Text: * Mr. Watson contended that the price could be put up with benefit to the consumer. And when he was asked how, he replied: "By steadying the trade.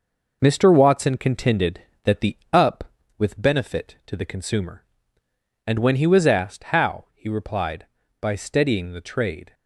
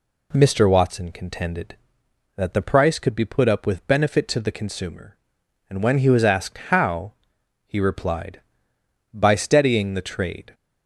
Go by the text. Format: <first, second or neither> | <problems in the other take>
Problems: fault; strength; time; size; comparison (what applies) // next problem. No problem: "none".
second | skips "price could be put"; at 2.4 s